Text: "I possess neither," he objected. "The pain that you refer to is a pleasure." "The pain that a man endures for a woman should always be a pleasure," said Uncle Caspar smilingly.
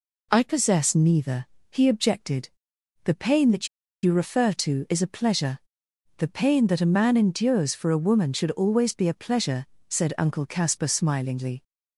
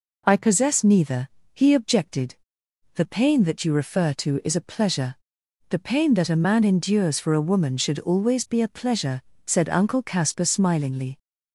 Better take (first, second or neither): second